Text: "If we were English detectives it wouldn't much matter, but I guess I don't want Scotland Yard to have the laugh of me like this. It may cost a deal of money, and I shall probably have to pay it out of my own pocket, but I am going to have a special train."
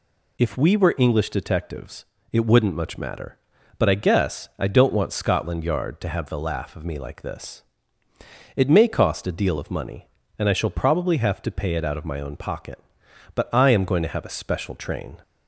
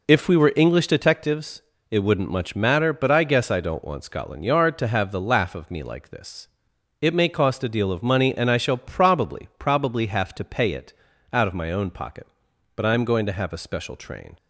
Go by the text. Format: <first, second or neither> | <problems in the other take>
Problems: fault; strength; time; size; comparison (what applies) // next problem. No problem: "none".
first | pauses between "detectives" and "it"; slight; at 1.6 s; 0.26 s long; slight in the first // says "probably" twice; at 9.5 s // pauses between "it" and "out"; at 10.9 s; 0.40 s long